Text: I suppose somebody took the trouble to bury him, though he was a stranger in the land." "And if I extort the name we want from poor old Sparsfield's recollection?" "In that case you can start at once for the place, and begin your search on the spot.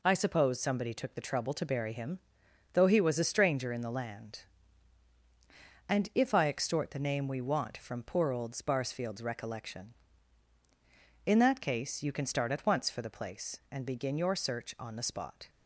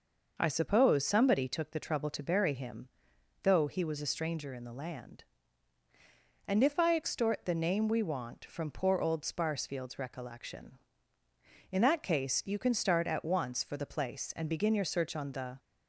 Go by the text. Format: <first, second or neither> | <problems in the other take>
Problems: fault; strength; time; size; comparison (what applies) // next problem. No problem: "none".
first | stops before "spot"; at 15.5 s